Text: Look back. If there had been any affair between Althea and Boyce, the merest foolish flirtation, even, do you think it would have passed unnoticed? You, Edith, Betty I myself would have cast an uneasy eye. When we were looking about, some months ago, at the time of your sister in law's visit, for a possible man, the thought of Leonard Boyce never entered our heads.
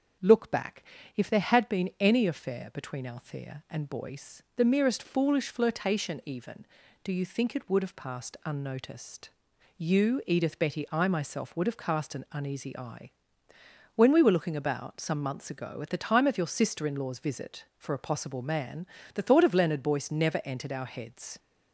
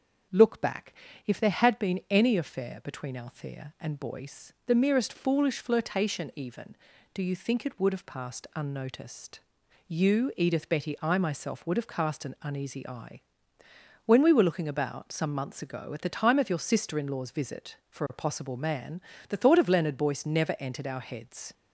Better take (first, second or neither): neither